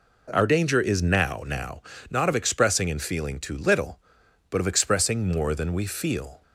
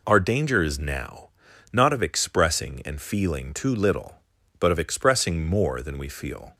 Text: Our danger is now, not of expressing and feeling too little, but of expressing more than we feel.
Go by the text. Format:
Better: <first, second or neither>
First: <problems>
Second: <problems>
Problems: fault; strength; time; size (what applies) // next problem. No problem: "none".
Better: second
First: says "now" twice; at 1.4 s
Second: none